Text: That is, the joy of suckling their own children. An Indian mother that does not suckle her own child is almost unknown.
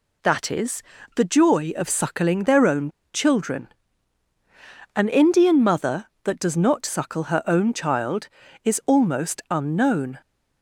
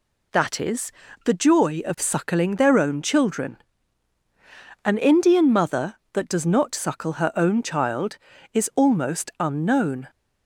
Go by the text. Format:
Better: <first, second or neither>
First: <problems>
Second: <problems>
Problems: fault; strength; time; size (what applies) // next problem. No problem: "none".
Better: second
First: pauses between "own" and "children"; slight; at 2.8 s; 0.24 s long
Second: none